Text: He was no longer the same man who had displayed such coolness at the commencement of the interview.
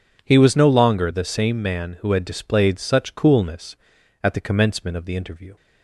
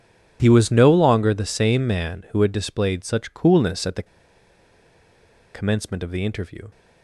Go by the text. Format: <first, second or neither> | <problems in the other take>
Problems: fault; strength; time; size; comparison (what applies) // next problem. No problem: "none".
first | pauses between "the" and "commencement"; strong; at 4.0 s; 1.4 s long